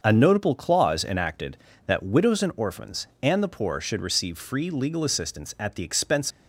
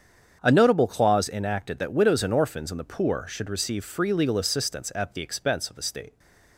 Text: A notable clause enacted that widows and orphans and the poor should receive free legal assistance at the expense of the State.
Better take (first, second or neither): second